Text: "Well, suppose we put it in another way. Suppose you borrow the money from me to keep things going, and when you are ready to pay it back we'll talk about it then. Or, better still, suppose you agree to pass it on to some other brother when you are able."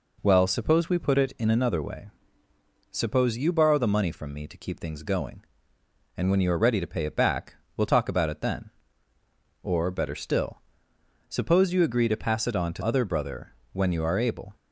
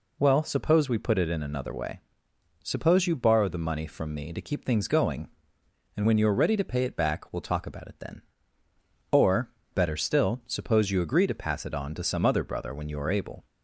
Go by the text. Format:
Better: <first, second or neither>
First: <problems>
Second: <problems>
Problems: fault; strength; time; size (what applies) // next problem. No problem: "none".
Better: second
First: pauses between "back" and "we'll"; slight; at 7.5 s; 0.22 s long // skips "some"; at 12.8 s // pauses between "brother" and "when"; slight; at 13.5 s; 0.18 s long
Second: none